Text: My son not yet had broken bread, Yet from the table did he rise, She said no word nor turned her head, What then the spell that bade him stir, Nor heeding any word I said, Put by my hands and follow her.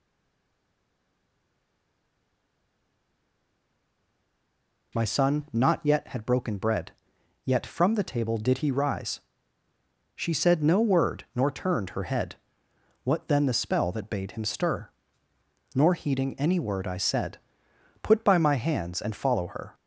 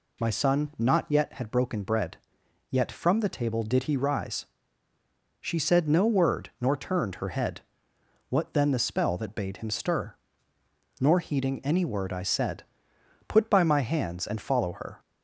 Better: second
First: stays silent before the first word; strong; until 4.9 s; 4.9 s long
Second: none

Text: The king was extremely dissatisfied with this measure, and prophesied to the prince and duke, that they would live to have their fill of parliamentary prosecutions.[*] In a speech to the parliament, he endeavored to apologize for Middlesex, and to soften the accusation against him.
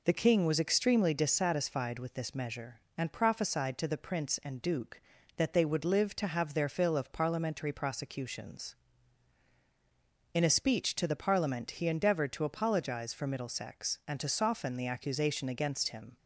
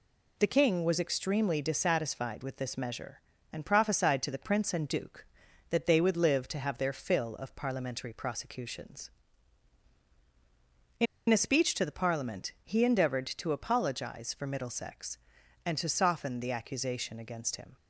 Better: first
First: none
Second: pauses between "In" and "a"; slight; at 11.0 s; 0.24 s long

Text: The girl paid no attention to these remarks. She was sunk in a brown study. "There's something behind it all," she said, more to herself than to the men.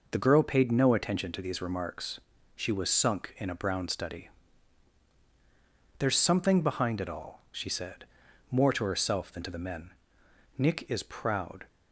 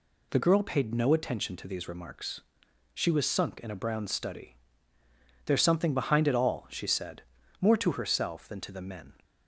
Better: second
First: goes on to say "Nick is proud"; noticeable; from 10.5 s on; 1.1 s long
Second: none

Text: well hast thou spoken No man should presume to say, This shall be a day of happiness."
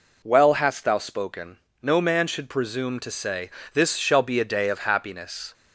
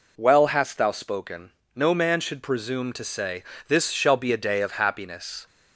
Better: neither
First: pauses between "spoken" and "No"; slight; at 1.5 s; 0.24 s long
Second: pauses between "spoken" and "No"; slight; at 1.4 s; 0.24 s long

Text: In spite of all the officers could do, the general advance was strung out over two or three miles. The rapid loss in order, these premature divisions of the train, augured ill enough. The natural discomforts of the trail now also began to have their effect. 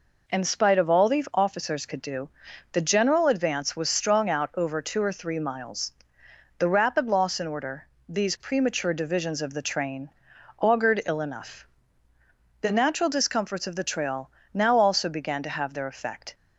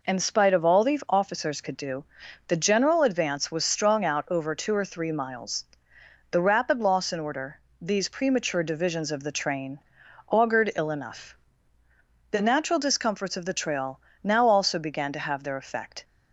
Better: neither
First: pauses between "trail" and "now"; slight; at 14.2 s; 0.24 s long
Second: pauses between "trail" and "now"; slight; at 13.9 s; 0.24 s long

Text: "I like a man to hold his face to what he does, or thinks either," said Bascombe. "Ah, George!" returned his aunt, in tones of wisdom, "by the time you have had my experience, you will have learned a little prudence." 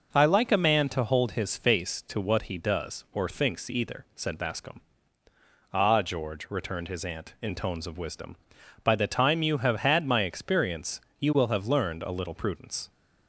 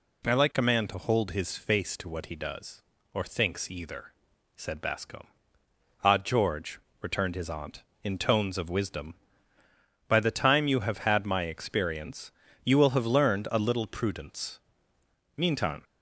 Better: first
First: none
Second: goes on to say "Meantime"; slight; from 15.3 s on; 0.46 s long

